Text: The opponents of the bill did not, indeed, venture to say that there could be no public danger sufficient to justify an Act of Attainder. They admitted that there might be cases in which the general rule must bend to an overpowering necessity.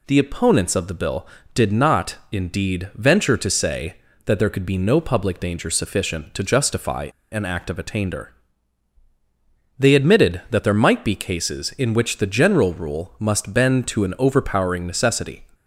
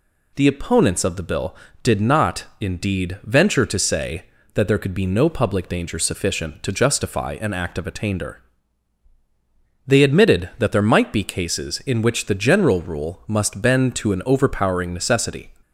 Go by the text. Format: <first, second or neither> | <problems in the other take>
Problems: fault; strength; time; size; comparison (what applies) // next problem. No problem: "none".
second | pauses between "justify" and "an"; slight; at 7.0 s; 0.23 s long